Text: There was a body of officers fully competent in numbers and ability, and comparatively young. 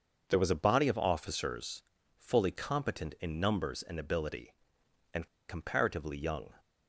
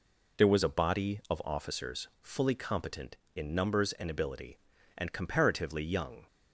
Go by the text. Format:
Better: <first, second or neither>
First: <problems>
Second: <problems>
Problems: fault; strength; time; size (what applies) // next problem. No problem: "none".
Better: second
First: starts louder than the rest; until 1.3 s; 6.5 dB // pauses between "officers" and "fully"; slight; at 1.8 s; 0.36 s long // pauses between "and" and "comparatively"; slight; at 5.2 s; 0.20 s long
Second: none